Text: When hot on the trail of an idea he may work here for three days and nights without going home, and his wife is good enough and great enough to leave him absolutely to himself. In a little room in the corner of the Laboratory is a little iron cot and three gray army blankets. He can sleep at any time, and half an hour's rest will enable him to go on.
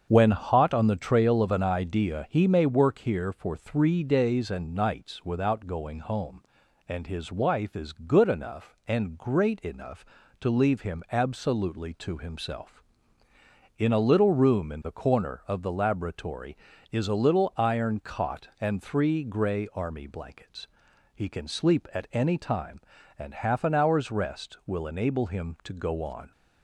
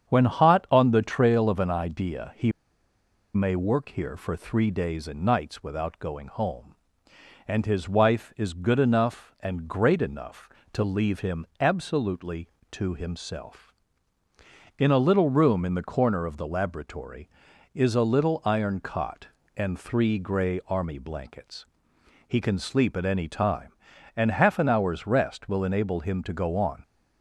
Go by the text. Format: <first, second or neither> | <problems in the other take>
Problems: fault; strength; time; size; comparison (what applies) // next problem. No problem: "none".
first | starts louder than the rest; strong; until 1.1 s; 8 dB; also in the first // pauses between "he" and "may"; noticeable; at 2.5 s; 0.84 s long